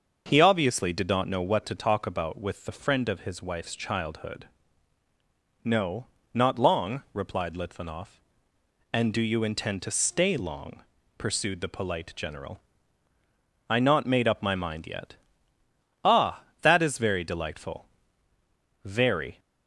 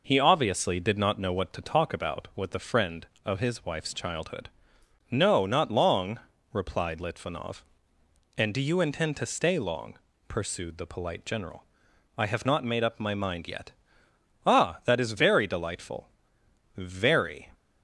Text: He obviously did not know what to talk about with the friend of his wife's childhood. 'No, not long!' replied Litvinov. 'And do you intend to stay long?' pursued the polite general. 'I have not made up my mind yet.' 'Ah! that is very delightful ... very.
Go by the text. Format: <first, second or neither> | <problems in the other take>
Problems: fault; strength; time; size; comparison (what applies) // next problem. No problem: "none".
second | starts louder than the rest; until 1.2 s; 6.5 dB // skips "have"; at 13.7 s